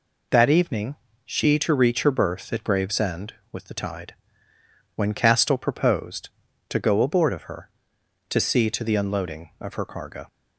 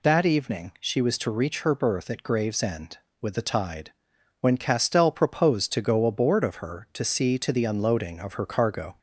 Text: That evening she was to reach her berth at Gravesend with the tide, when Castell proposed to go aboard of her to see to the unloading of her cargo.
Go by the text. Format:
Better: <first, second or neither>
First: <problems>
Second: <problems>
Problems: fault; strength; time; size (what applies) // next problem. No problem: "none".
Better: second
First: pauses between "evening" and "she"; slight; at 0.9 s; 0.28 s long // skips "was"; at 1.5 s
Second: none